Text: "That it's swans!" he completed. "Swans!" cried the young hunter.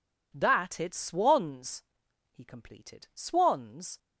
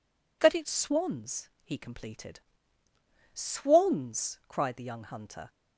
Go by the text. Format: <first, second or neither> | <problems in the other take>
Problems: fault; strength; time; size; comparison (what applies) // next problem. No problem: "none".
second | stops before "cried the young hunter"; at 3.9 s